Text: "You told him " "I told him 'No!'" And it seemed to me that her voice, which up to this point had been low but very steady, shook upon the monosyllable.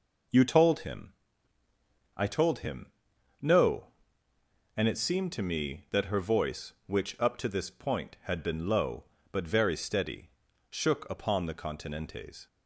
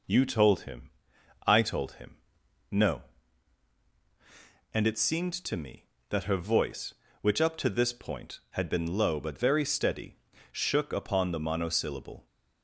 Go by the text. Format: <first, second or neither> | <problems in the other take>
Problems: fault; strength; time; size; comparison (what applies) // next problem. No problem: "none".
second | pauses between "him" and "No"; noticeable; at 2.9 s; 0.48 s long; noticeable in the second // says "continentes" for "monosyllable"; at 11.5 s